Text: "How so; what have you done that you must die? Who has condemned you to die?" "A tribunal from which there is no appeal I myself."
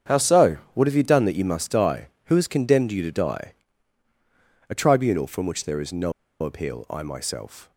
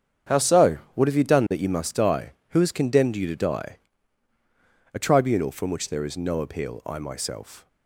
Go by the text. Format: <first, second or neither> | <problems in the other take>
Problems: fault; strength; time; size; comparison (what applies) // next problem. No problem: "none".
second | starts louder than the rest; strong; until 1.2 s; 8 dB; strong in the second // pauses between "no" and "appeal"; slight; at 6.1 s; 0.30 s long